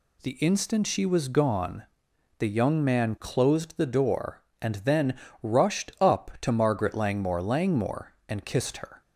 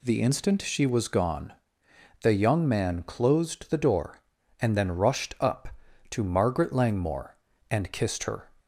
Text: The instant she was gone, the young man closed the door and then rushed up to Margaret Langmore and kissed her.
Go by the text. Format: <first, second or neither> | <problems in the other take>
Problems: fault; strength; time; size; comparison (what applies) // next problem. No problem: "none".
second | pauses between "then" and "rushed"; slight; at 5.1 s; 0.26 s long // says "Langmore" twice; at 7.4 s